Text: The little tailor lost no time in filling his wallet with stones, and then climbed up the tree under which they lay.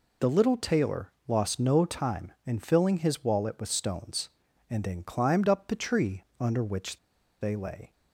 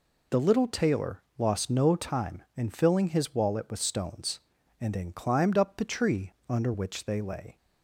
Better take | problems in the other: second | pauses between "tailor" and "lost"; slight; at 1.1 s; 0.16 s long; slight in the second // pauses between "tree" and "under"; slight; at 6.2 s; 0.16 s long; slight in the second // pauses between "which" and "they"; at 6.9 s; 0.43 s long

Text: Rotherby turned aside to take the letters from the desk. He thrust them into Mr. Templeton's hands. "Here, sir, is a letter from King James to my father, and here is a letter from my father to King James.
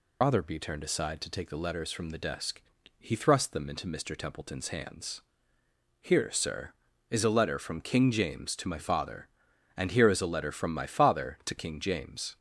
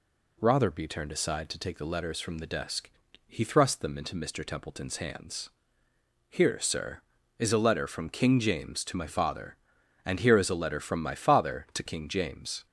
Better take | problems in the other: second | loses the start of "Rotherby"; at 0.2 s; 95 ms

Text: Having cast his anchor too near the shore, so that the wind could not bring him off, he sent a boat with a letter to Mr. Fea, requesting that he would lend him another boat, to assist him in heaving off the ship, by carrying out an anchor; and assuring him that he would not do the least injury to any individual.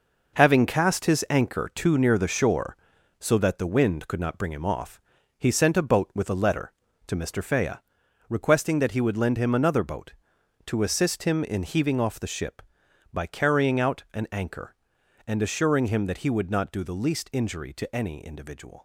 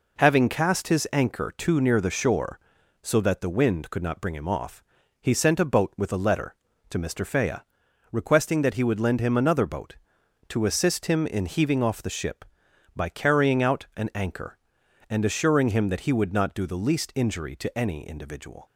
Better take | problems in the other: second | gets quieter; strong; throughout; 8.5 dB

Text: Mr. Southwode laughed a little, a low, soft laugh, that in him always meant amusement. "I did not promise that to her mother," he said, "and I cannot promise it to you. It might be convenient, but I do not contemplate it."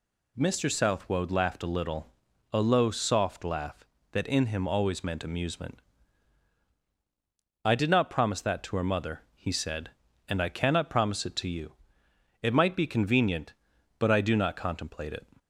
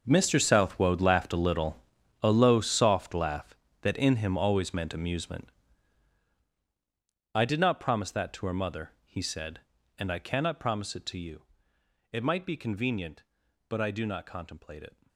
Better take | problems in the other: first | gets quieter; strong; throughout; 14 dB

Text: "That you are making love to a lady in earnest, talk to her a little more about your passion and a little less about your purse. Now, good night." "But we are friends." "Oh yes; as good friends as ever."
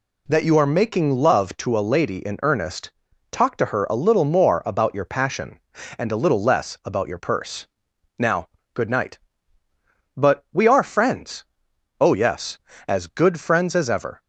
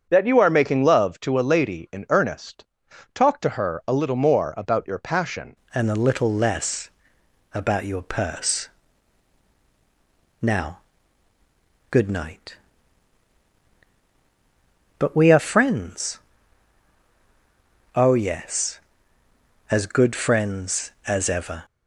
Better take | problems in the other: first | starts louder than the rest; strong; until 1.1 s; 7 dB // changes voice at "and"; from 5.7 s on; 15.9 s long // pauses between "less" and "about"; noticeable; at 6.8 s; 0.64 s long

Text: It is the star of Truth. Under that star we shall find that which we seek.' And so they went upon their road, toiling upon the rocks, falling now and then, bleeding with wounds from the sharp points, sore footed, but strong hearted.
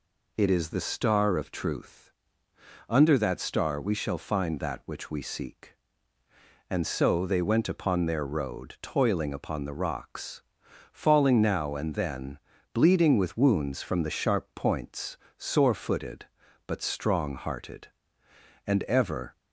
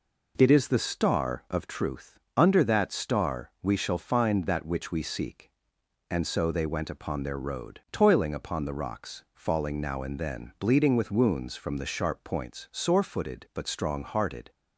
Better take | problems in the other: second | goes on to say "And ever"; noticeable; from 18.6 s on; 0.70 s long

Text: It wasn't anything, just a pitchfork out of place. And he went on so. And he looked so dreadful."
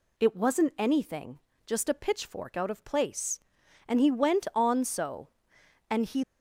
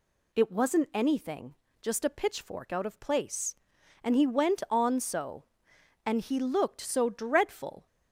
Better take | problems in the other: second | stops before "looked so dreadful"; at 6.2 s

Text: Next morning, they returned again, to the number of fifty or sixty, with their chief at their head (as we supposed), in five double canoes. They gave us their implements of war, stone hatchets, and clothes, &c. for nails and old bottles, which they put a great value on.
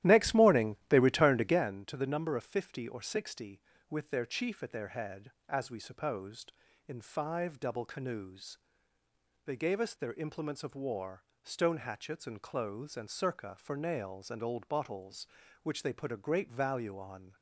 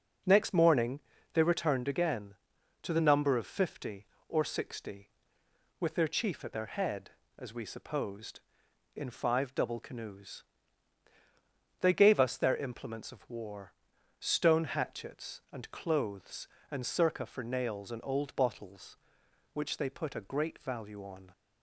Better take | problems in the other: second | starts louder than the rest; strong; until 1.6 s; 13 dB

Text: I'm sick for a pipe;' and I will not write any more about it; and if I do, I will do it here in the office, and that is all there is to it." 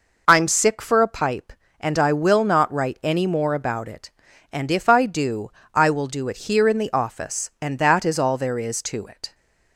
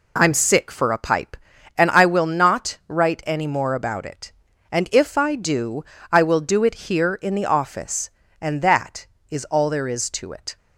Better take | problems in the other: neither | none

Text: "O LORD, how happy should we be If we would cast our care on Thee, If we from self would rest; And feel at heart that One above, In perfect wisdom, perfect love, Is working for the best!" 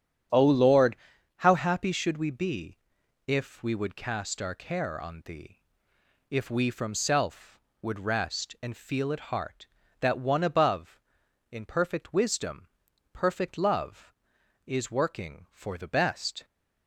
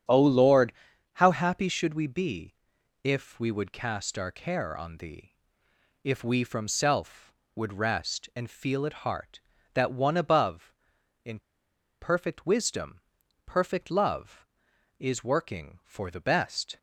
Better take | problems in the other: first | starts louder than the rest; strong; until 1.5 s; 9 dB; strong in the first // pauses between "be" and "If"; noticeable; at 2.5 s; 0.48 s long; noticeable in the first // pauses between "In" and "perfect"; noticeable; at 11.4 s; 0.60 s long

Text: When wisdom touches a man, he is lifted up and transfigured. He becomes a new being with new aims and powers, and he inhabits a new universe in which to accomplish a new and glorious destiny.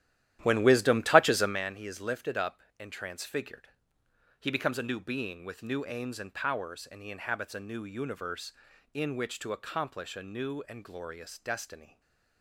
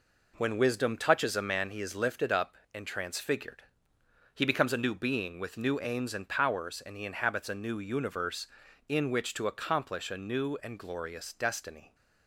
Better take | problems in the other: second | starts louder than the rest; strong; until 1.6 s; 12.5 dB // stays silent after the last word; slight; from 11.8 s on; 0.6 s long

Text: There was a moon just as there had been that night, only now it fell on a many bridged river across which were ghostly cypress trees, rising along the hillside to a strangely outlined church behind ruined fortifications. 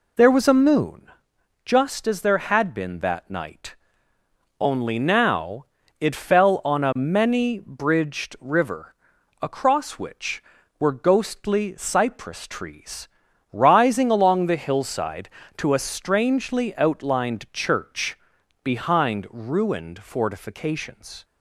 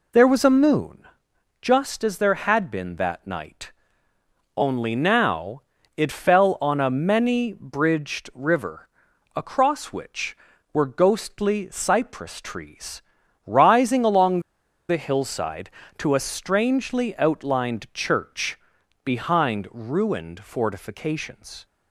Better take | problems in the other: first | pauses between "moon" and "just"; noticeable; at 1.0 s; 0.56 s long; noticeable in the first // pauses between "now" and "it"; slight; at 5.6 s; 0.36 s long; slight in the first // pauses between "river" and "across"; noticeable; at 8.8 s; 0.48 s long; noticeable in the first // pauses between "along" and "the"; noticeable; at 14.3 s; 0.49 s long // pauses between "church" and "behind"; noticeable; at 18.5 s; 0.46 s long; noticeable in the first

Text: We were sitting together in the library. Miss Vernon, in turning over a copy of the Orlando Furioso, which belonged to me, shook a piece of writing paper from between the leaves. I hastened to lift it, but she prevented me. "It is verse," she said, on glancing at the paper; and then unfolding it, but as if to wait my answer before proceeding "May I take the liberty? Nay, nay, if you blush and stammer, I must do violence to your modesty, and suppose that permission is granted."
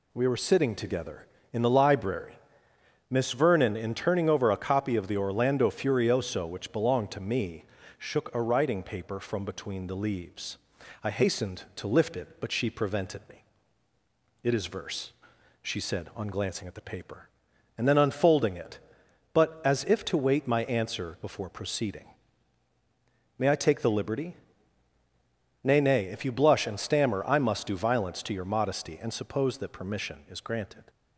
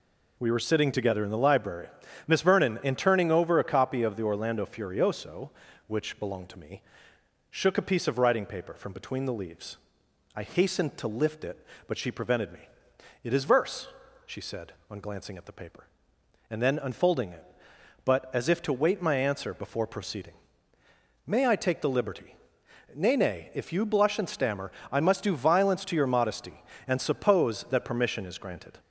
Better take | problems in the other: second | skips "piece of"; at 8.4 s // pauses between "proceeding" and "May"; strong; at 22.0 s; 1.3 s long; noticeable in the second

